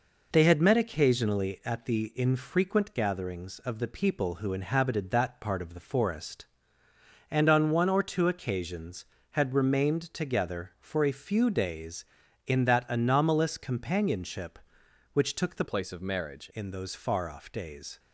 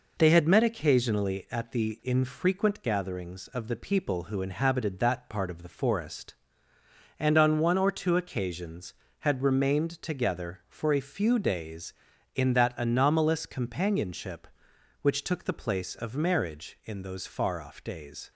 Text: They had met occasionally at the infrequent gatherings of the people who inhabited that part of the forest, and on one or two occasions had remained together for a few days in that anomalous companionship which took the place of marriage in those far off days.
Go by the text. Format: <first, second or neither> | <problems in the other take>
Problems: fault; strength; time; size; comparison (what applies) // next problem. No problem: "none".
second | changes voice from "place" to "marriage"; from 15.6 to 16.4 s; 0.8 s long